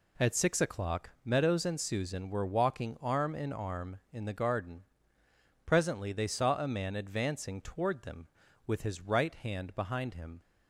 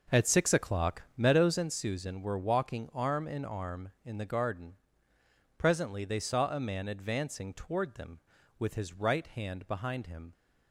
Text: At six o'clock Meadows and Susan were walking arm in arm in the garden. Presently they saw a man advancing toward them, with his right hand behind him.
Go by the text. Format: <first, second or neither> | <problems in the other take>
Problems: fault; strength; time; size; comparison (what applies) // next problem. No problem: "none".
first | starts louder than the rest; noticeable; until 1.7 s; 6 dB // pauses between "o'clock" and "Meadows"; slight; at 1.0 s; 0.16 s long; slight in the first